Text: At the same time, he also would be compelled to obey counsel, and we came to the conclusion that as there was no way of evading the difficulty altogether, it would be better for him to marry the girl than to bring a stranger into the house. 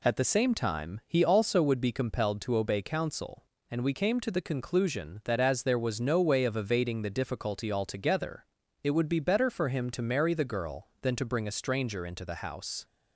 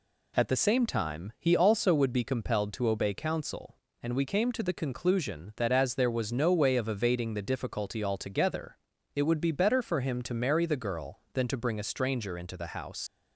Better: first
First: none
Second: leaves "house" unfinished; at 13.0 s; 100 ms

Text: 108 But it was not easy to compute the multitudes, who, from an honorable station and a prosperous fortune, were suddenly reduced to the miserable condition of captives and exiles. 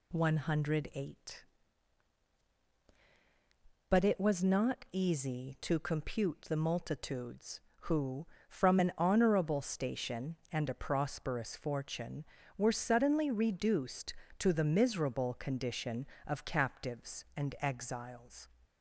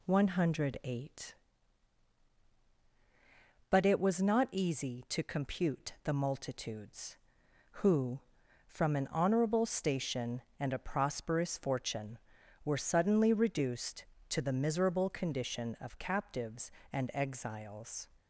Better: neither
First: none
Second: none

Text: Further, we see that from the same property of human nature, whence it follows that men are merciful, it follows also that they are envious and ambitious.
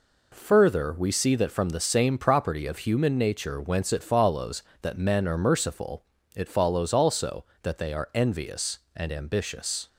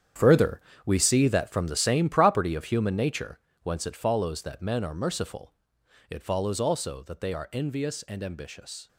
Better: first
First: none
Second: gets quieter; strong; throughout; 12.5 dB

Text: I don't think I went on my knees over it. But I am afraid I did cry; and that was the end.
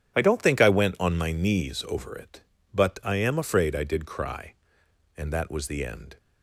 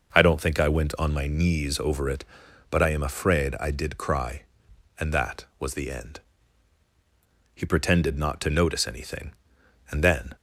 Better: first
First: none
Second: goes on to say "He pretended not to notice anything and then"; strong; from 7.5 s on; 2.8 s long

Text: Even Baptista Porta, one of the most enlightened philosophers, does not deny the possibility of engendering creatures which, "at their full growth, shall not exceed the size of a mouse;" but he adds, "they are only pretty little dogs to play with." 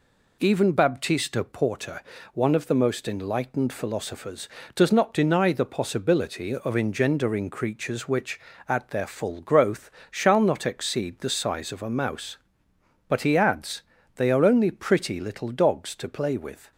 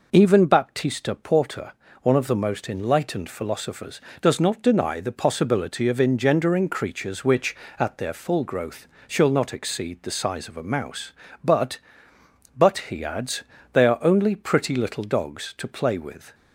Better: first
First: none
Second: says "but" twice; at 12.5 s

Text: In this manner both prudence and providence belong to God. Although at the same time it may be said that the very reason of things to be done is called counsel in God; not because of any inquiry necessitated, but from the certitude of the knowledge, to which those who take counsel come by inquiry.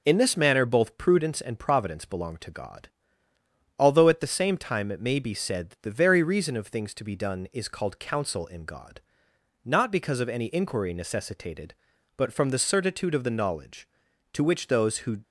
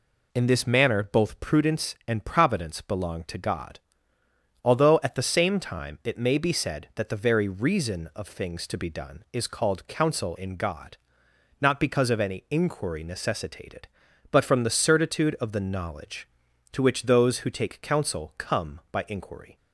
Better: second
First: stops before "take counsel come by inquiry"; at 15.2 s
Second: none

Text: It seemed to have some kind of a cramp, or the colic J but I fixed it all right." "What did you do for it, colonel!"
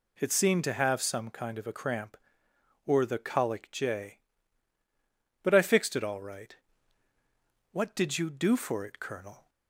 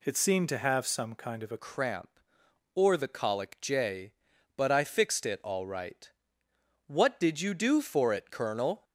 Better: first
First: none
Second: changes voice at "cramp"; from 1.5 s on; 7.3 s long

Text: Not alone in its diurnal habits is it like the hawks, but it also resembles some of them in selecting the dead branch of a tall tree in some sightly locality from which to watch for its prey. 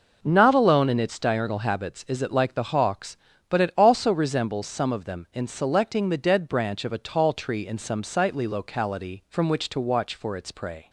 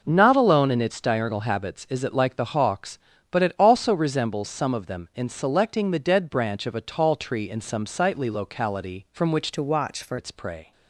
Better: first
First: none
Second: changes voice from "to" to "for"; from 9.5 to 10.1 s; 0.6 s long

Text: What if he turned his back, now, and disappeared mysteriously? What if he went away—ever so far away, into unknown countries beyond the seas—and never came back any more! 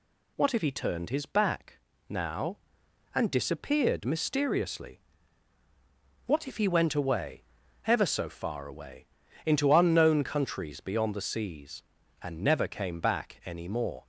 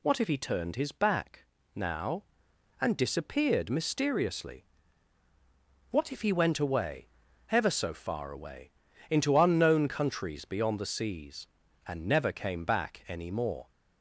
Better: neither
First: none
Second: none

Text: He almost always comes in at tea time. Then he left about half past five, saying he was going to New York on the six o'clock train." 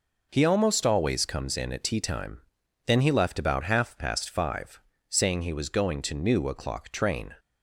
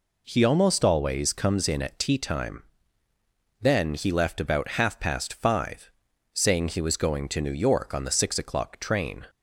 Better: second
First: skips "York on the six"; at 6.4 s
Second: none

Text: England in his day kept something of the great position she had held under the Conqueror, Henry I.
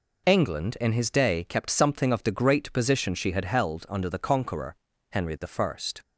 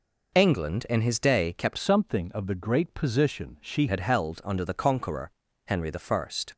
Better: first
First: pauses between "Henry" and "I"; slight; at 5.3 s; 0.21 s long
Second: changes voice from "something" to "she"; from 1.7 to 3.8 s; 2.1 s long // pauses between "Henry" and "I"; slight; at 5.9 s; 0.18 s long

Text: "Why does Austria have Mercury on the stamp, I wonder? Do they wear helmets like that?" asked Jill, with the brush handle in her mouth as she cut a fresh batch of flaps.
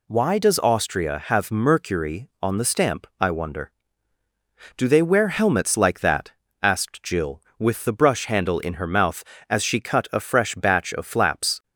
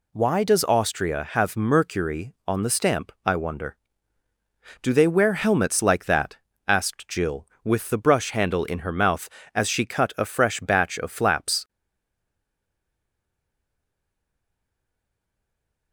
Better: first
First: none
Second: stays silent after the last word; strong; from 11.6 s on; 4.3 s long

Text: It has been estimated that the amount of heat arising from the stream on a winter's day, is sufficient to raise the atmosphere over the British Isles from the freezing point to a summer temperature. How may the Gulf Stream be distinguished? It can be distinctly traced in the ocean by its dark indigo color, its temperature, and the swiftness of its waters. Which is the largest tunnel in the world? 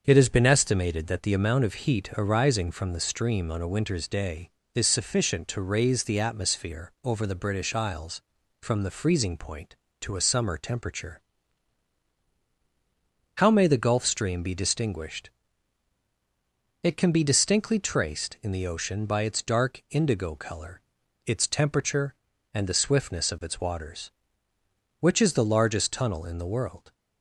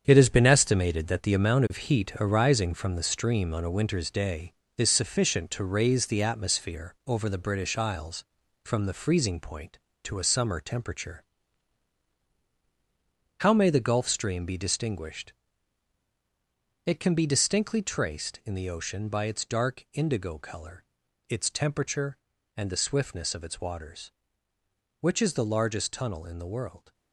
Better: first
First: starts louder than the rest; until 1.0 s; 7 dB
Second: gets quieter; strong; throughout; 8.5 dB // starts louder than the rest; strong; until 1.0 s; 8 dB

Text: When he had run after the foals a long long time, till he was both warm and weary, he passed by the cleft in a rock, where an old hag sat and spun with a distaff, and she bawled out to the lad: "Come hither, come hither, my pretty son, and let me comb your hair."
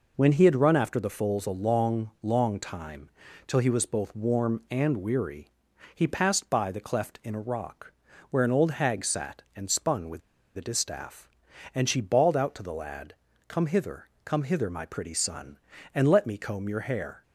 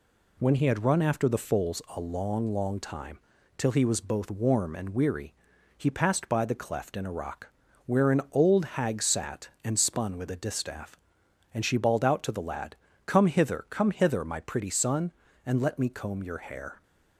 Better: second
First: pauses between "with" and "a"; at 10.2 s; 0.37 s long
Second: none

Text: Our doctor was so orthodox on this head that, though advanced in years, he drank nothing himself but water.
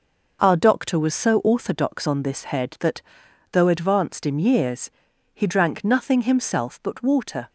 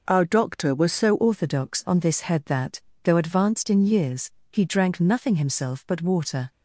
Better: first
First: none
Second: changes voice at "orthodox"; from 1.1 s on; 5.4 s long

